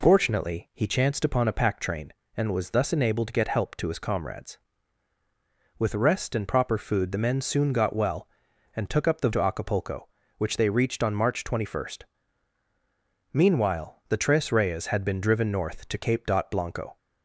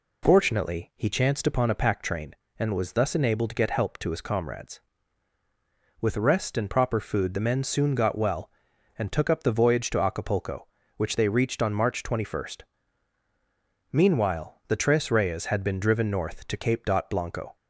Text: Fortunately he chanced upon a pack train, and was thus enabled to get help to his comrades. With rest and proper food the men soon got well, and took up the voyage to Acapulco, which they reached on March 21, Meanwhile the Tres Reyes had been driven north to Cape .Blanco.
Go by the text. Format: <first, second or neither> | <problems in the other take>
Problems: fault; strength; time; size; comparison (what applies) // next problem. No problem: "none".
second | skips "voyage"; at 9.3 s